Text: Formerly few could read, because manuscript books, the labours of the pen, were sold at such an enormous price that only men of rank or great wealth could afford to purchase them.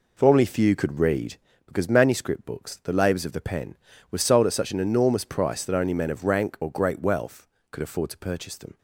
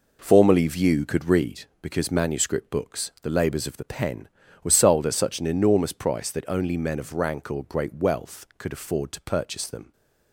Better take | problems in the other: first | says "view" for "few"; at 0.6 s

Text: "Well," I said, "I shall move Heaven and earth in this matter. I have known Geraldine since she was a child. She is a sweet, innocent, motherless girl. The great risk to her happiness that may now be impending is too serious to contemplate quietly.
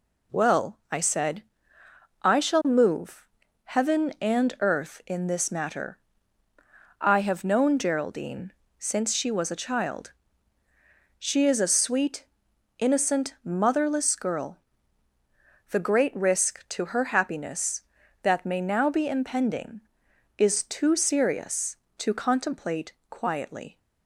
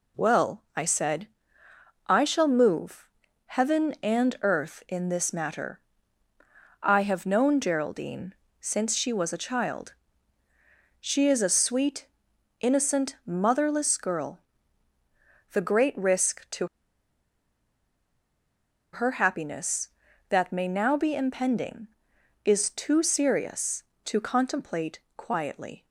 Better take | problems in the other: first | pauses between "move" and "Heaven"; at 3.0 s; 0.38 s long; also in the first // pauses between "Geraldine" and "since"; slight; at 8.3 s; 0.26 s long; slight in the first // pauses between "to" and "her"; strong; at 16.6 s; 2.2 s long // pauses between "contemplate" and "quietly"; slight; at 24.9 s; 0.16 s long; slight in the first

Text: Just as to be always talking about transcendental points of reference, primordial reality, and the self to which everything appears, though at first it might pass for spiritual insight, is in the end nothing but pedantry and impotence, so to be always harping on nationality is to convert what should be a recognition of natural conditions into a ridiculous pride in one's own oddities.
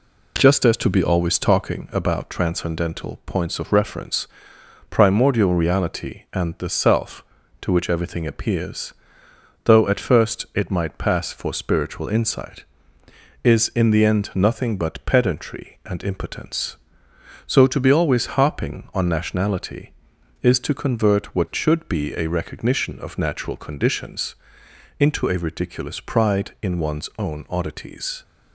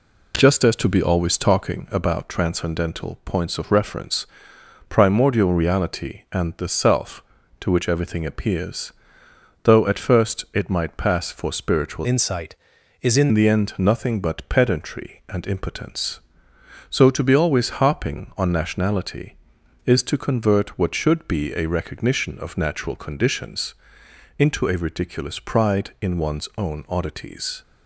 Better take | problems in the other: first | changes voice from "insight" to "in"; from 12.0 to 13.2 s; 1.2 s long // pauses between "conditions" and "into"; noticeable; at 23.7 s; 0.66 s long; noticeable in the first

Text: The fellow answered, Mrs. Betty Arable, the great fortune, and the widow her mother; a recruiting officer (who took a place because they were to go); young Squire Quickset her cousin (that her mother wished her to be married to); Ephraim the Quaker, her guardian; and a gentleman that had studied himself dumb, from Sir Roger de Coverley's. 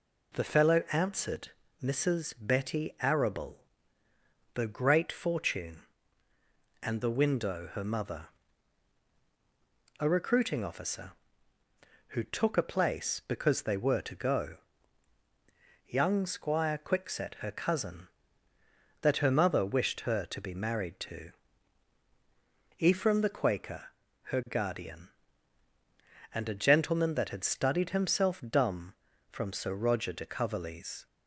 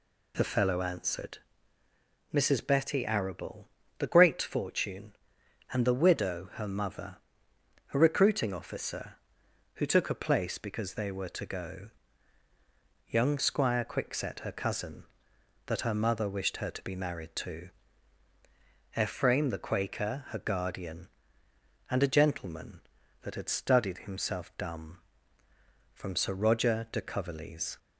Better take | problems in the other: second | says "window" for "widow"; at 7.1 s

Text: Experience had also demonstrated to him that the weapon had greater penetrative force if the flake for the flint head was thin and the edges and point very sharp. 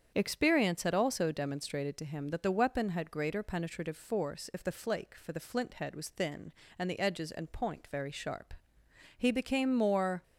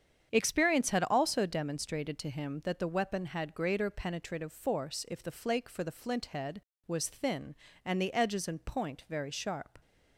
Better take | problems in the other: second | starts louder than the rest; strong; until 1.1 s; 8 dB; strong in the second // goes on to say "He became more"; noticeable; from 9.1 s on; 1.0 s long

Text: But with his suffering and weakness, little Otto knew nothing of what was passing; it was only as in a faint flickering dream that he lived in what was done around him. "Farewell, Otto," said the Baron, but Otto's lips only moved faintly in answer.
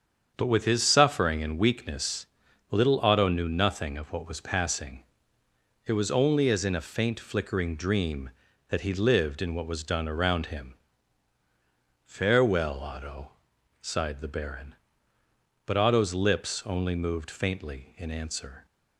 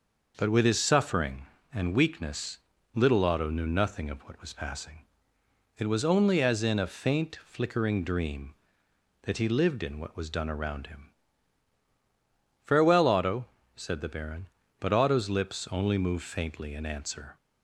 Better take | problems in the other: second | starts louder than the rest; strong; until 1.3 s; 7.5 dB // says "sighed" for "said"; at 13.7 s

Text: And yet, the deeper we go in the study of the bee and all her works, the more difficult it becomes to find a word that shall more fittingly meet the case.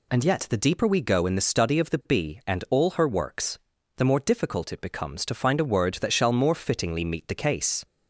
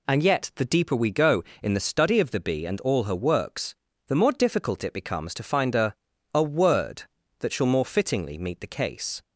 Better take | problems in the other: first | says "a" twice; at 6.3 s

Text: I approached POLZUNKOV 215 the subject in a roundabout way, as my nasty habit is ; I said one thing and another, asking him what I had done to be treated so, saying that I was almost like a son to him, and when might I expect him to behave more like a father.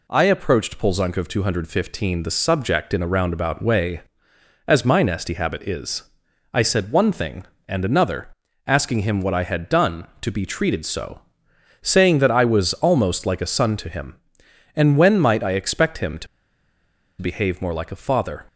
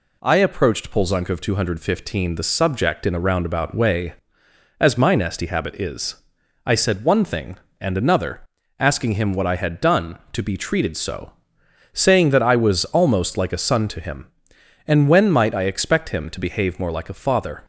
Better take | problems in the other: second | pauses between "to" and "behave"; noticeable; at 16.2 s; 0.94 s long

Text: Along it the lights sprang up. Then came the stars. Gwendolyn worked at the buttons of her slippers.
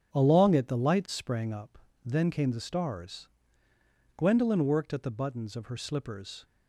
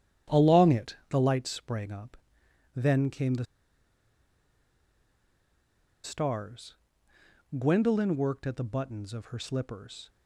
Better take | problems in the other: first | starts louder than the rest; strong; until 1.4 s; 9.5 dB; strong in the first // pauses between "the" and "stars"; strong; at 3.4 s; 2.5 s long

